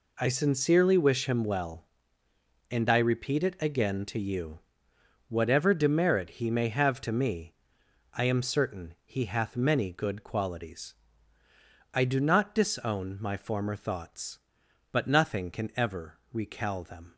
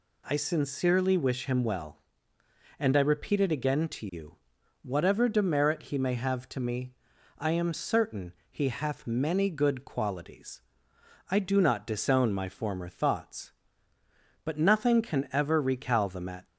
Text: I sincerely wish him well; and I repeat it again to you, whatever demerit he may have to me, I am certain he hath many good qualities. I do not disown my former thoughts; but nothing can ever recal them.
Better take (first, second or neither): first